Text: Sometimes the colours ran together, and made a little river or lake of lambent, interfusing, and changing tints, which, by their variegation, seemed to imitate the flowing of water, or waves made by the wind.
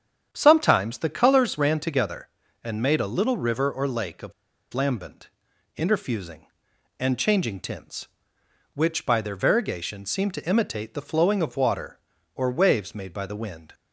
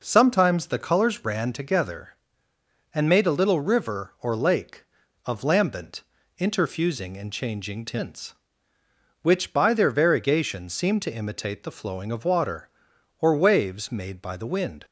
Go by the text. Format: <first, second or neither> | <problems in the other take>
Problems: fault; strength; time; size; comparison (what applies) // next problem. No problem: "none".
second | starts louder than the rest; strong; until 1.3 s; 8.5 dB // pauses between "of" and "lambent"; at 4.3 s; 0.41 s long